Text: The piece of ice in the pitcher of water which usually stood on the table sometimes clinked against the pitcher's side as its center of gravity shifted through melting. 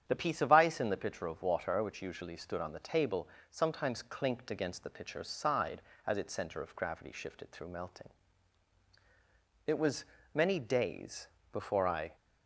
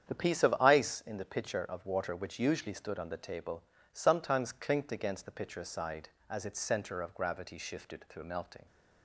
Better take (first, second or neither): second